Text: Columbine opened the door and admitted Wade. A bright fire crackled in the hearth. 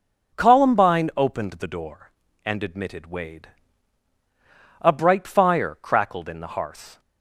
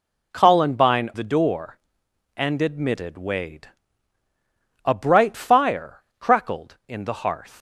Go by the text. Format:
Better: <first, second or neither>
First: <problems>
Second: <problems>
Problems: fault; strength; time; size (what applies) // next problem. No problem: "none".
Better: first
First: none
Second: skips "opened"; at 1.1 s // pauses between "fire" and "crackled"; slight; at 6.0 s; 0.18 s long